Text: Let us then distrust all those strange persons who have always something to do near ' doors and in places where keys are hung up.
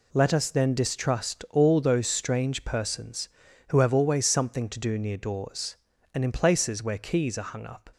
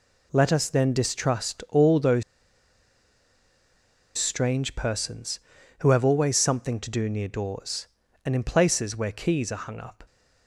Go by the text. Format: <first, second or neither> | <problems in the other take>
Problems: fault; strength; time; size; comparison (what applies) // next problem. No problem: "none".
first | pauses between "those" and "strange"; strong; at 2.2 s; 1.9 s long